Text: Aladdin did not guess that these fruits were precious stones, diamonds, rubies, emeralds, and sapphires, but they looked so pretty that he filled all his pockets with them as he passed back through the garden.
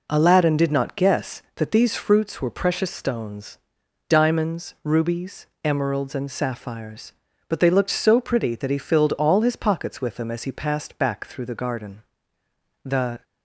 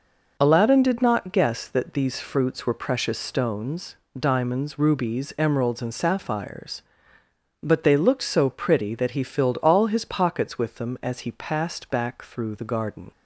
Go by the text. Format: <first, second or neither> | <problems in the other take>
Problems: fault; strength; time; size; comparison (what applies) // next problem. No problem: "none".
second | goes on to say "The"; slight; from 12.8 s on; 0.40 s long